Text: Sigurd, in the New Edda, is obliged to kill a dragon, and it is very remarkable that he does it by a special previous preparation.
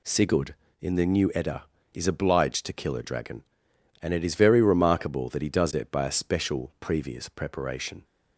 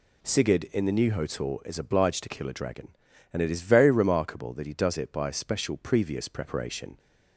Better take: first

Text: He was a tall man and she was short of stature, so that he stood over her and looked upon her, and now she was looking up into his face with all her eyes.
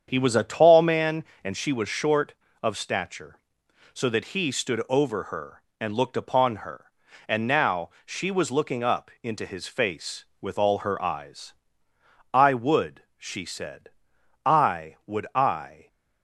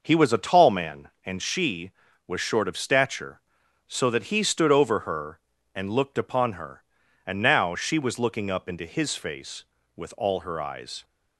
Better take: second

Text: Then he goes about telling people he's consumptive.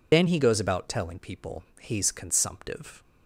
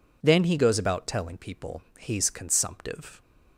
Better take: second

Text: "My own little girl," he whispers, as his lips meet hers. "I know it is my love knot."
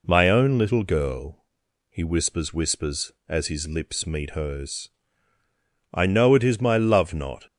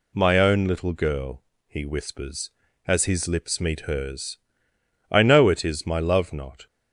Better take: second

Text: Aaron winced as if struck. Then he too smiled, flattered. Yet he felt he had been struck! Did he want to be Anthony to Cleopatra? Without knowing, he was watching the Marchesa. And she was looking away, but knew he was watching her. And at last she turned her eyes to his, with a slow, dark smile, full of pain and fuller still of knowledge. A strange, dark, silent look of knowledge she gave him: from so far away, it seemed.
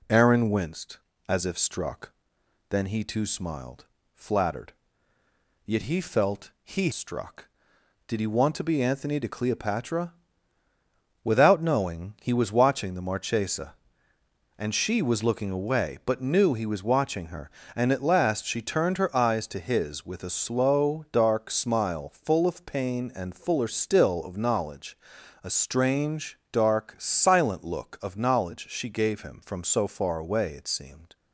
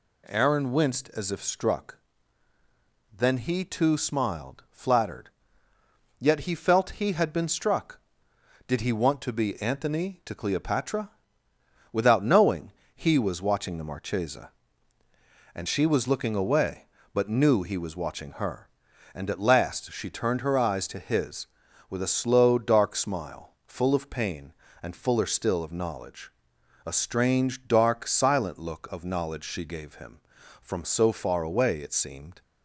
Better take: second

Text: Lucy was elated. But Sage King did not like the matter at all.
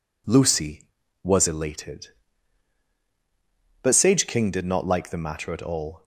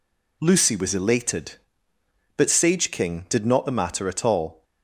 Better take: first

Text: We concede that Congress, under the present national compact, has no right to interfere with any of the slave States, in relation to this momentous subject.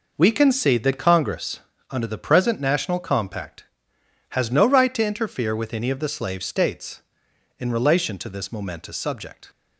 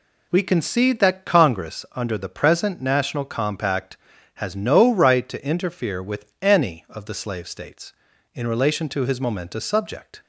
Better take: first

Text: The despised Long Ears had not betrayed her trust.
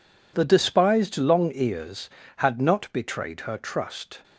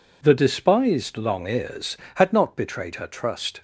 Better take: neither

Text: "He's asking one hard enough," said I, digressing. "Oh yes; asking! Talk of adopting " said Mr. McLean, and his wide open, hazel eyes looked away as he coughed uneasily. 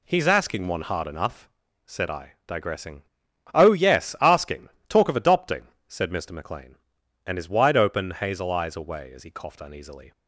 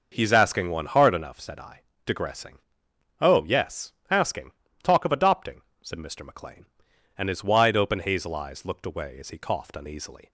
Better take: second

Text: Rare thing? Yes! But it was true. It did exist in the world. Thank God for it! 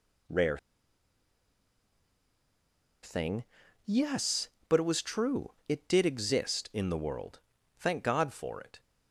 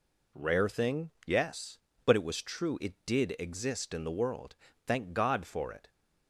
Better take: second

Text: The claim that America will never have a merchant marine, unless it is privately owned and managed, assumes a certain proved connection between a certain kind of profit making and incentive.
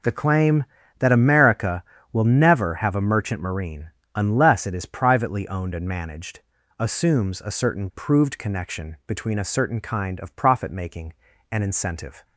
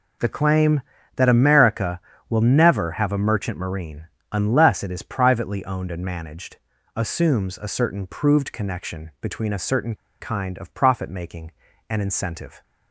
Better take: first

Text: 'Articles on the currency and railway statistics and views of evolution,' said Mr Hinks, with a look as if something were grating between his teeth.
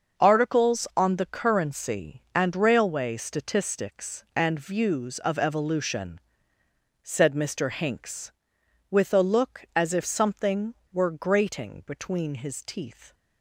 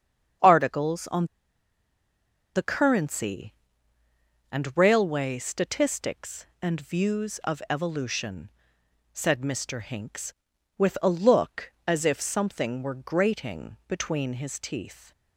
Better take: first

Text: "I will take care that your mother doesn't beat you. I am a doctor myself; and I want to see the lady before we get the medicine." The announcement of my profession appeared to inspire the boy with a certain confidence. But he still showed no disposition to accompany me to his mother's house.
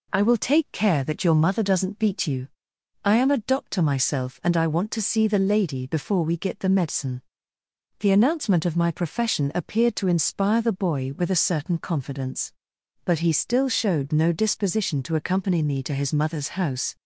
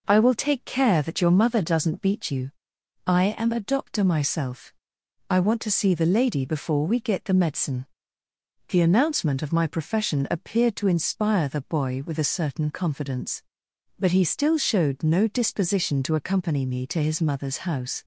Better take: first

